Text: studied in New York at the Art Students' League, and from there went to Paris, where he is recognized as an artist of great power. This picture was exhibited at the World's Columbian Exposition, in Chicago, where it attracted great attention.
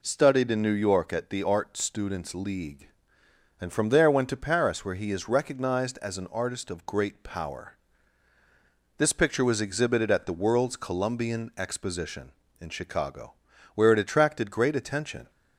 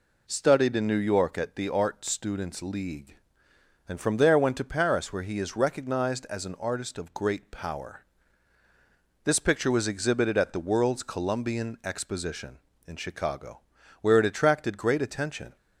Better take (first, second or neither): neither